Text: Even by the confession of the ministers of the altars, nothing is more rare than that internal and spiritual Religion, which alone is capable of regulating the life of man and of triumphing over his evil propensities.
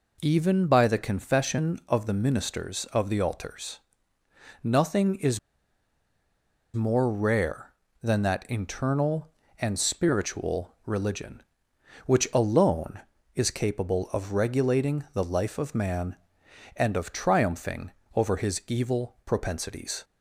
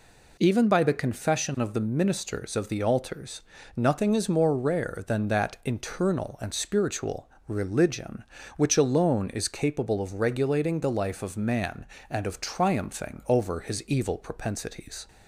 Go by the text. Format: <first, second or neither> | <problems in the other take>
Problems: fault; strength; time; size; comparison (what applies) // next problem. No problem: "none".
second | pauses between "is" and "more"; strong; at 5.3 s; 1.3 s long // pauses between "spiritual" and "Religion"; slight; at 10.6 s; 0.16 s long; slight in the second // pauses between "triumphing" and "over"; slight; at 17.8 s; 0.24 s long